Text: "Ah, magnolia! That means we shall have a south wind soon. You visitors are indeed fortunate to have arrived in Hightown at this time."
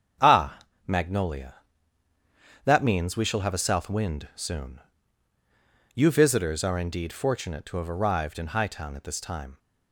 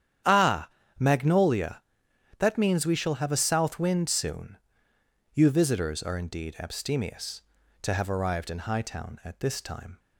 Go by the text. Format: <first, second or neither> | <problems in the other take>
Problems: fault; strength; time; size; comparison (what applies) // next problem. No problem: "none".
first | starts louder than the rest; strong; until 1.5 s; 9.5 dB; strong in the first // says "abstemious" for "fortunate"; at 6.5 s